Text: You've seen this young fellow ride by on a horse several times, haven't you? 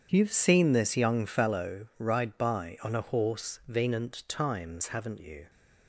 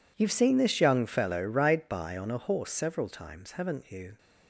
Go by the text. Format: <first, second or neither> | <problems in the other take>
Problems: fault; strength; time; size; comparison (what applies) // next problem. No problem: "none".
second | starts louder than the rest; strong; until 1.1 s; 8 dB // says "venant" for "several"; at 3.6 s